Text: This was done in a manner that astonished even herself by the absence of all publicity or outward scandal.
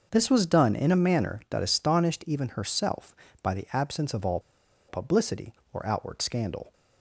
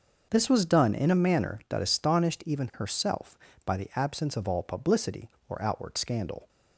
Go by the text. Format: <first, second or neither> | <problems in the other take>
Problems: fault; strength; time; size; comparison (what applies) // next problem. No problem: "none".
second | starts louder than the rest; noticeable; until 1.1 s; 6 dB; noticeable in the second // pauses between "all" and "publicity"; noticeable; at 4.3 s; 0.49 s long